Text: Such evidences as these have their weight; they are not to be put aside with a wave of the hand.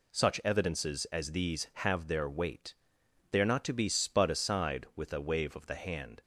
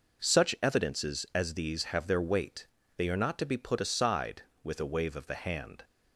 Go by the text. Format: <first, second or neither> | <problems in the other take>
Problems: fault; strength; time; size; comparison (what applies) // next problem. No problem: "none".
second | says "spud" for "put"; at 3.8 s